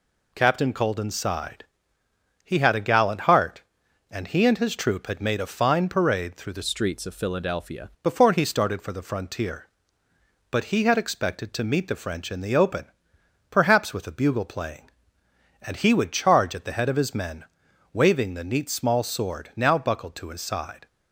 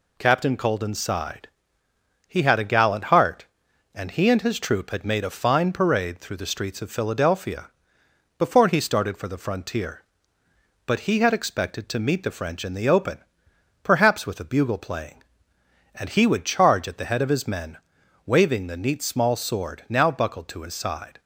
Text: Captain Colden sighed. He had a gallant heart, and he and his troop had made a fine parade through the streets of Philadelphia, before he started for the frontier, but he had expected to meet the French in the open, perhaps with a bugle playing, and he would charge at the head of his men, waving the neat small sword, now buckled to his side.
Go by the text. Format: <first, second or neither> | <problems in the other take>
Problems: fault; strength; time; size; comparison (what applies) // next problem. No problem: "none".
second | changes voice from "streets" to "Philadelphia"; from 6.6 to 7.8 s; 1.2 s long